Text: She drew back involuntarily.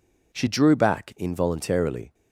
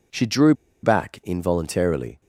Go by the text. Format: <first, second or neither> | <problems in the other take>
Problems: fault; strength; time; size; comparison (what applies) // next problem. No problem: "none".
first | pauses between "drew" and "back"; slight; at 0.5 s; 0.29 s long